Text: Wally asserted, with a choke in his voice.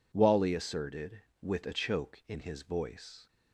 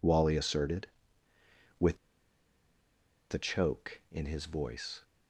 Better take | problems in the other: first | pauses between "with" and "a"; strong; at 1.9 s; 1.3 s long

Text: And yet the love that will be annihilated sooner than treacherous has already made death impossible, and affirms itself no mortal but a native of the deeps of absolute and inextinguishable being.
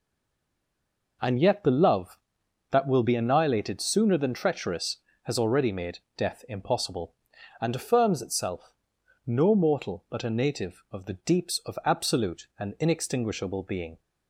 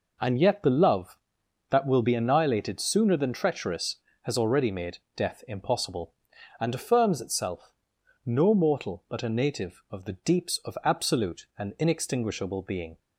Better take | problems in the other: second | stays silent before the first word; noticeable; until 1.2 s; 1.2 s long // pauses between "made" and "death"; slight; at 5.9 s; 0.18 s long; slight in the second // pauses between "itself" and "no"; noticeable; at 8.7 s; 0.54 s long; noticeable in the second

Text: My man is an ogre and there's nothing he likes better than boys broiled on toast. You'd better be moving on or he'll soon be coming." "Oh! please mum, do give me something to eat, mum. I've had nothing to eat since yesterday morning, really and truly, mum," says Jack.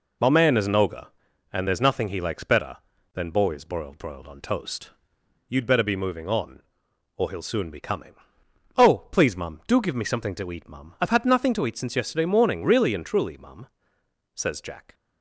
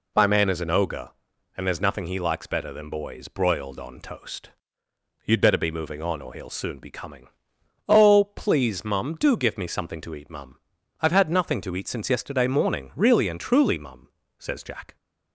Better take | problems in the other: second | says "broiled" twice; at 3.9 s

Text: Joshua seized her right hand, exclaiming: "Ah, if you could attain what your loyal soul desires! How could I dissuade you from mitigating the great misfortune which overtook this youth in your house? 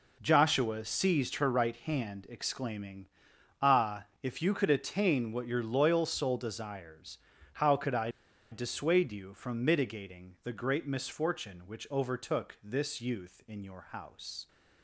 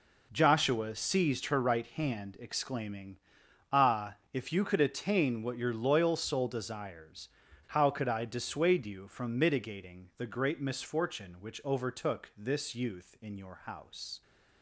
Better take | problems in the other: second | pauses between "I" and "dissuade"; at 8.0 s; 0.42 s long

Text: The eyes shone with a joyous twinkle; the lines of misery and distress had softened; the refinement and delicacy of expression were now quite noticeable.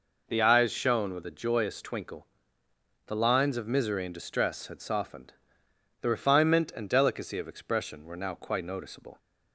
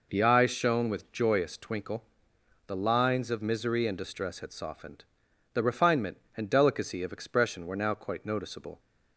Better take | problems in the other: first | skips "a"; at 1.1 s

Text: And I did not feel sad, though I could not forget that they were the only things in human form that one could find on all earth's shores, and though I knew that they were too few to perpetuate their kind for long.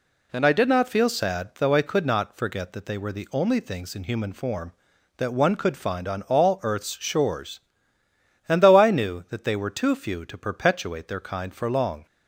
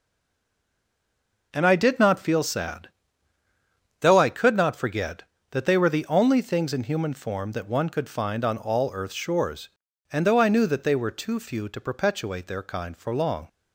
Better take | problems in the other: first | stays silent before the first word; noticeable; until 1.5 s; 1.5 s long

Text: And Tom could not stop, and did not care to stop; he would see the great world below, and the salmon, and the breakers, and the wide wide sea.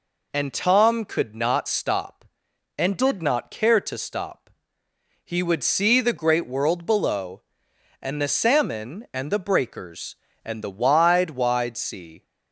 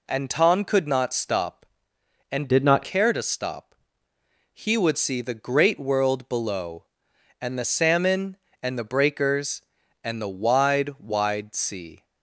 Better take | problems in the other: first | changes voice from "did" to "not"; from 2.4 to 2.8 s; 0.4 s long

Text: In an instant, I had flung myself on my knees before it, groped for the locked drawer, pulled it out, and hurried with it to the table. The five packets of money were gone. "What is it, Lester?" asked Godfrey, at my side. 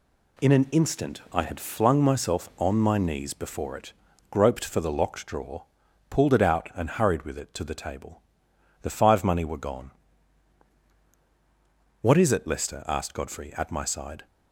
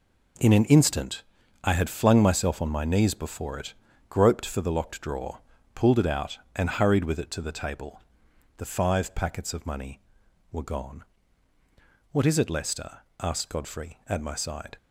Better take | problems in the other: second | skips "packets of"; at 9.2 s

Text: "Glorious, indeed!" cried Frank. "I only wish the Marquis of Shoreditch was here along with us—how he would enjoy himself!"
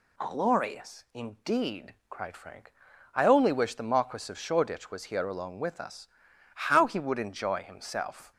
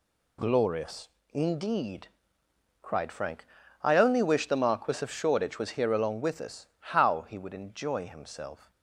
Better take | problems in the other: neither | none

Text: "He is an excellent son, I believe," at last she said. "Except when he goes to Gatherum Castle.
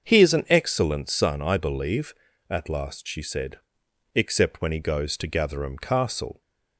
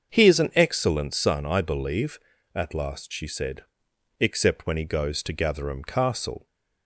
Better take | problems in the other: neither | starts louder than the rest; the same in both

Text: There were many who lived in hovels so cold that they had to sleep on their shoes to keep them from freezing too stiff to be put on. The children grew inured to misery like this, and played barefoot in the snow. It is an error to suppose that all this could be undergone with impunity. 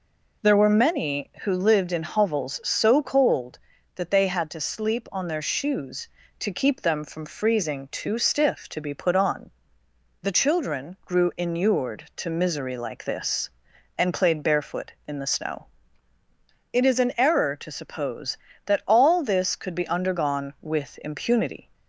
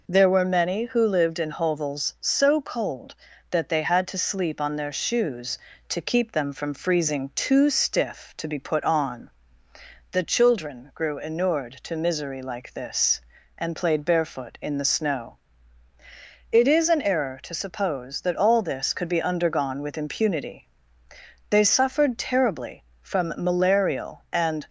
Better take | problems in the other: first | goes on to say "They suffered terribly from malarial and"; strong; from 21.4 s on; 3.1 s long

